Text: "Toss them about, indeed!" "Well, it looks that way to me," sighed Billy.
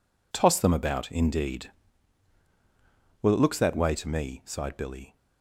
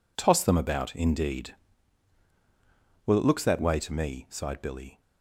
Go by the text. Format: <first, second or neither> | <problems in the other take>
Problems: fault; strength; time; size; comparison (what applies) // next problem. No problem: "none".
neither | none